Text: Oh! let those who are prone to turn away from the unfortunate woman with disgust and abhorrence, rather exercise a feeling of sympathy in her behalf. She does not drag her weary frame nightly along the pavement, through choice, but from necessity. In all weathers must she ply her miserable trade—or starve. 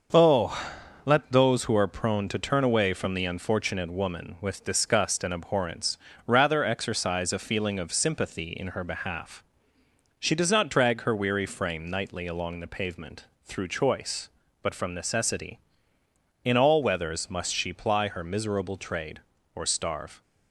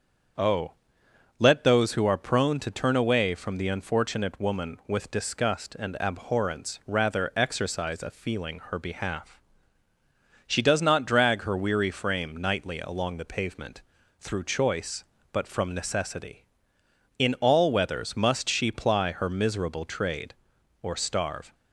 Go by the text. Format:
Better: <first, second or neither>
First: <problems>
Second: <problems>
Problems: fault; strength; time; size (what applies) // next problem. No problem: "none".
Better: first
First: starts louder than the rest; until 1.5 s; 6.5 dB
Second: starts louder than the rest; strong; until 2.0 s; 7 dB // skips "of sympathy in"; at 8.6 s